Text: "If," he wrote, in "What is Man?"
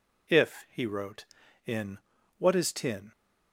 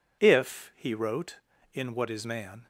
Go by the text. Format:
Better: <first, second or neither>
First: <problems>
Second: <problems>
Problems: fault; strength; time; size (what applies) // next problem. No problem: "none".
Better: second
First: pauses between "in" and "What"; at 1.9 s; 0.40 s long // says "Tin" for "Man"; at 2.7 s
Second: none